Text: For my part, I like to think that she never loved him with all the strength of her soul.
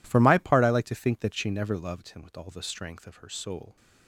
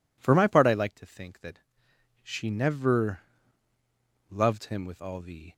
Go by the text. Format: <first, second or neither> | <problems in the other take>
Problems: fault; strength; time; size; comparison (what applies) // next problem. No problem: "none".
first | pauses between "that" and "she"; noticeable; at 1.6 s; 0.62 s long // pauses between "never" and "loved"; at 3.2 s; 1.0 s long // stops before "strength of her soul"; at 5.5 s